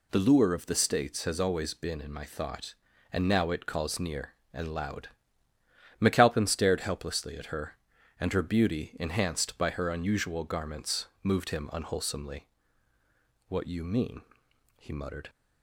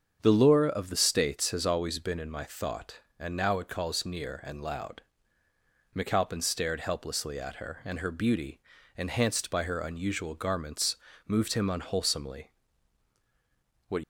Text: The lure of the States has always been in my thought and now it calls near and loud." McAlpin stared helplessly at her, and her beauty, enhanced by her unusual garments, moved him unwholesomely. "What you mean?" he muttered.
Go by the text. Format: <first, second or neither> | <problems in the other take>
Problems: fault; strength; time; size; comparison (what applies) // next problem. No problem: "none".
first | starts louder than the rest; until 1.2 s; 7 dB // stops before "you mean he muttered"; at 14.0 s